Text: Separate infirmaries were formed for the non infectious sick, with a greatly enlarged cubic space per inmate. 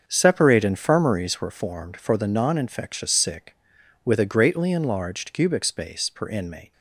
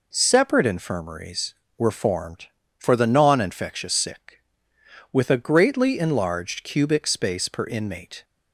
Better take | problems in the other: second | gets quieter; strong; throughout; 10 dB

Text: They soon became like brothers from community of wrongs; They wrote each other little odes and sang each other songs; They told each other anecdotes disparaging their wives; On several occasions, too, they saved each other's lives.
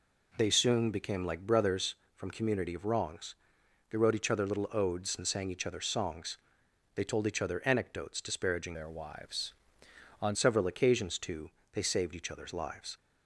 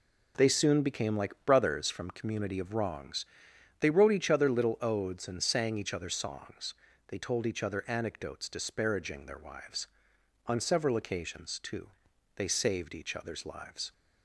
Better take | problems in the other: second | changes voice from "their" to "On"; from 8.7 to 10.3 s; 1.6 s long

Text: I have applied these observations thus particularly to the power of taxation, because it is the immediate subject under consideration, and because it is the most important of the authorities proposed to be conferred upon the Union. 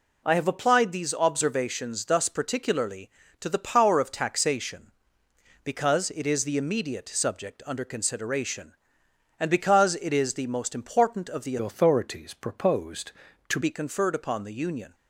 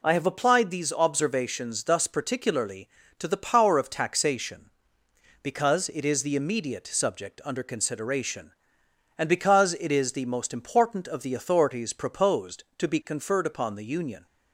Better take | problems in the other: second | changes voice from "authorities" to "to"; from 11.5 to 13.5 s; 2.0 s long

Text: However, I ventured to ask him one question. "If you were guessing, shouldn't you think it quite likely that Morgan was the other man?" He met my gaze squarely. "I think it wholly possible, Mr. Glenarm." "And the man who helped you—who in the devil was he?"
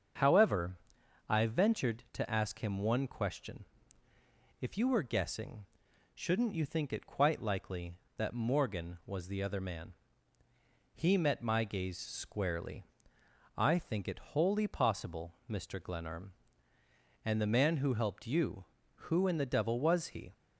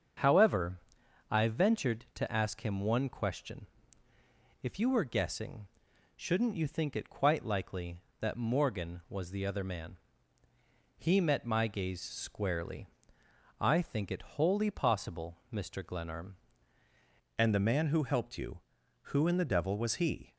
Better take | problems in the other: first | starts louder than the rest; strong; until 1.6 s; 7 dB; strong in the first // changes voice at "And"; from 17.3 s on; 3.0 s long

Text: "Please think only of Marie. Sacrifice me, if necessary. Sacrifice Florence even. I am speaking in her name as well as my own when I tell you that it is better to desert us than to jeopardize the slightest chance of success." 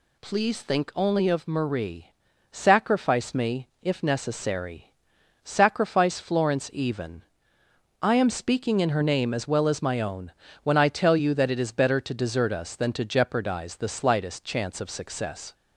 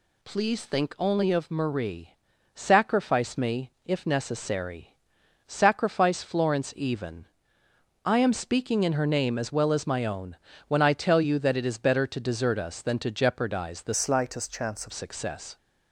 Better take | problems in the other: first | pauses between "own" and "when"; slight; at 10.3 s; 0.32 s long; slight in the first // changes voice from "slightest" to "of"; from 13.9 to 14.9 s; 1.0 s long

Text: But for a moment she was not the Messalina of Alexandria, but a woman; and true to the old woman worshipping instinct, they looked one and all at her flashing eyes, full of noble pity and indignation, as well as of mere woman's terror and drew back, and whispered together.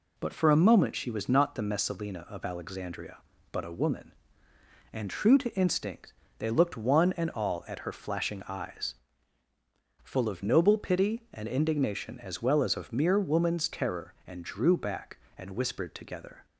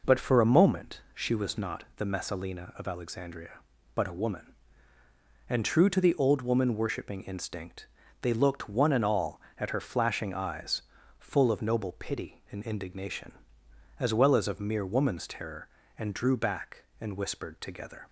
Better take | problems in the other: second | skips "the old woman worshipping"; at 5.5 s

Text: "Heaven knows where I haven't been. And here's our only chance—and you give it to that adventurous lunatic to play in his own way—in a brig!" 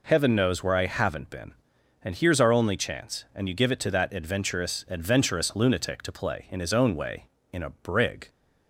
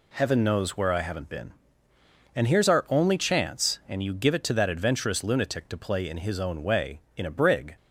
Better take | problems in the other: second | says "adventurous" twice; at 4.8 s

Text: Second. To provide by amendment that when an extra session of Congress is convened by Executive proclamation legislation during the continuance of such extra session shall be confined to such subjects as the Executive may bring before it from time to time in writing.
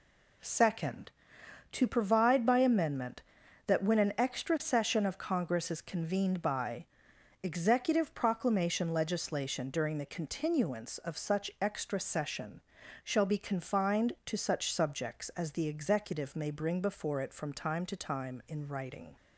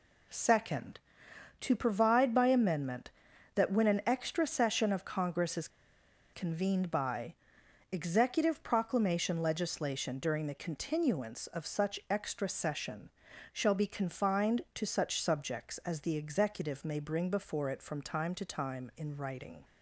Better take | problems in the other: first | pauses between "is" and "convened"; noticeable; at 5.6 s; 0.64 s long // pauses between "by" and "Executive"; noticeable; at 7.3 s; 0.58 s long; noticeable in the first // pauses between "session" and "shall"; at 13.0 s; 0.44 s long; also in the first

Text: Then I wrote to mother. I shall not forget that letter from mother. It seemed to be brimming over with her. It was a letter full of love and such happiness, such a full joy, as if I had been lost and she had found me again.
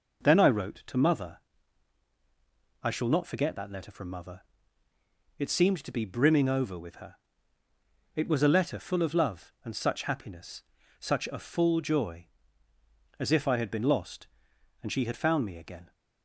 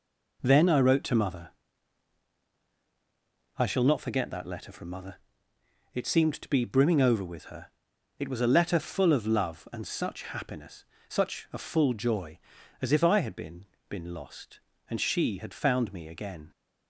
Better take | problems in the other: first | says "been" twice; at 13.9 s

